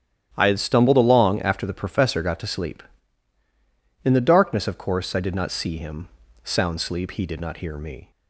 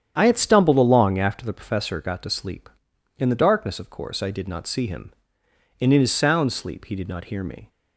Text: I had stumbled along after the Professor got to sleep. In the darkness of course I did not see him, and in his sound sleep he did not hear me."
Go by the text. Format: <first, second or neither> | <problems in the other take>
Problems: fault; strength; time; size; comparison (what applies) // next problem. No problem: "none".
second | starts louder than the rest; strong; until 1.3 s; 11 dB; strong in the second // skips "and in his"; at 6.2 s